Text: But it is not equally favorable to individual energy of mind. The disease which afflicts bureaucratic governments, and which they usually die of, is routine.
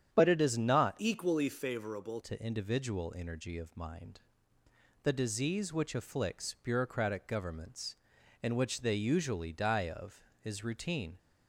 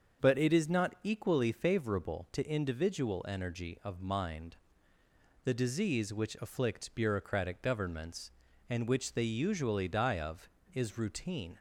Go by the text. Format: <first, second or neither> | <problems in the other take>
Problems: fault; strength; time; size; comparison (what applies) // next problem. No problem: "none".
second | starts louder than the rest; strong; until 1.1 s; 9 dB; also in the second // changes voice from "equally" to "favorable"; from 0.9 to 2.2 s; 1.3 s long